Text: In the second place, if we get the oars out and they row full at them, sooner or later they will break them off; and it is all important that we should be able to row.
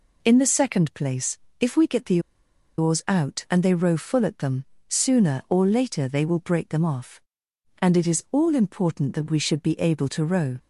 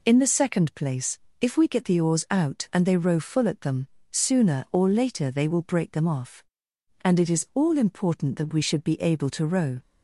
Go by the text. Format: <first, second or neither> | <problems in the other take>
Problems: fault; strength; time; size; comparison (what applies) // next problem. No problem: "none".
second | pauses between "the" and "oars"; noticeable; at 2.1 s; 0.58 s long